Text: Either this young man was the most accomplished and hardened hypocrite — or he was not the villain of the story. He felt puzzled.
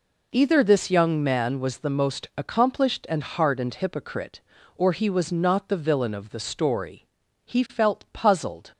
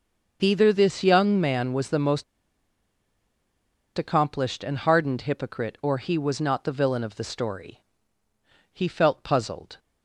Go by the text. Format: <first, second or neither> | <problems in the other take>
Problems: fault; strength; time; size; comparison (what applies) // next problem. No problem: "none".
first | starts louder than the rest; until 1.4 s; 6.5 dB // pauses between "most" and "accomplished"; strong; at 2.2 s; 1.7 s long